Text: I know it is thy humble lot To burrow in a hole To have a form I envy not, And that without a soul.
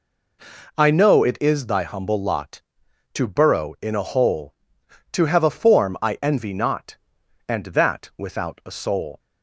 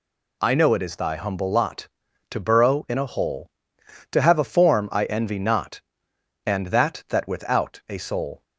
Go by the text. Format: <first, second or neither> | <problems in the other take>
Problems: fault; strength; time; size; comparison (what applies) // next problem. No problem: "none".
first | says "that" twice; at 7.0 s